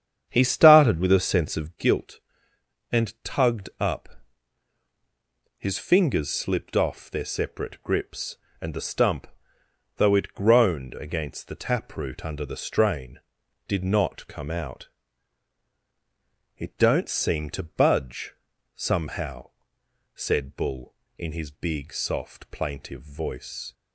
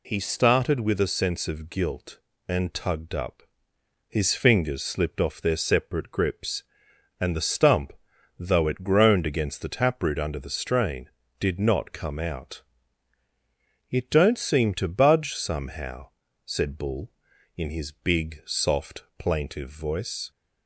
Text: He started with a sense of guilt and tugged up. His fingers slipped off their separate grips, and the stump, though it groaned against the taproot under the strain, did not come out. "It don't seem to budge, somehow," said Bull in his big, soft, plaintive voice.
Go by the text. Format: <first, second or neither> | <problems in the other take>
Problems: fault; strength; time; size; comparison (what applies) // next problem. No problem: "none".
second | starts louder than the rest; strong; until 1.9 s; 8.5 dB